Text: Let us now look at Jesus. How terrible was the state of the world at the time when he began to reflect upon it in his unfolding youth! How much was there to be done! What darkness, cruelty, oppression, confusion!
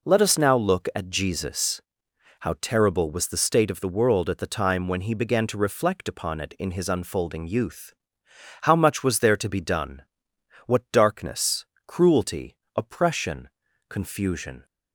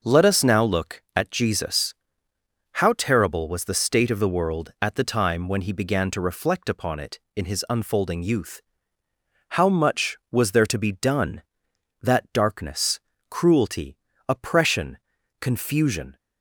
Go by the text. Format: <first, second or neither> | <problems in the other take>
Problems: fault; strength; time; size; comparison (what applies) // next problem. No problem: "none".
first | says "That" for "What"; at 12.0 s